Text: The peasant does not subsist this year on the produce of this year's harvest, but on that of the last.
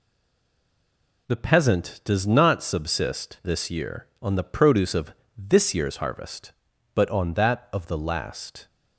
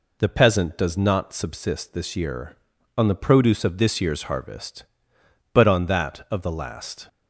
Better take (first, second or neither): second